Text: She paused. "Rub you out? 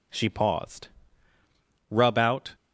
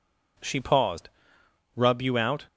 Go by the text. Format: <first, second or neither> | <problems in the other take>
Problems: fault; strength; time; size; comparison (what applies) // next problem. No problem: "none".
second | skips "you"; at 2.1 s